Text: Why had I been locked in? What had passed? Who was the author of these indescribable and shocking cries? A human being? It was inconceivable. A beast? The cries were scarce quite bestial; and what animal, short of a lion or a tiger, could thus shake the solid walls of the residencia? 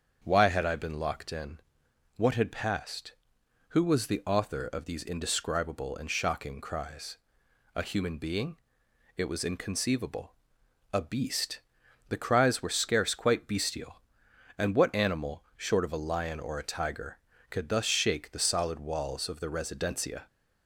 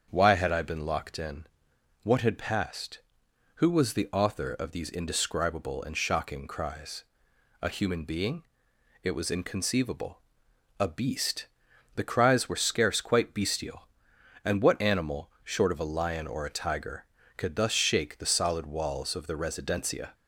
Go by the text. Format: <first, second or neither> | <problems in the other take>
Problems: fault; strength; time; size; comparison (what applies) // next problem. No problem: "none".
neither | starts louder than the rest; strong; the same in both